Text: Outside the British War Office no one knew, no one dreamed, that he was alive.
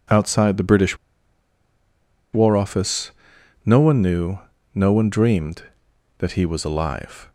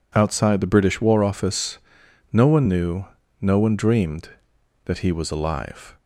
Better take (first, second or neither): second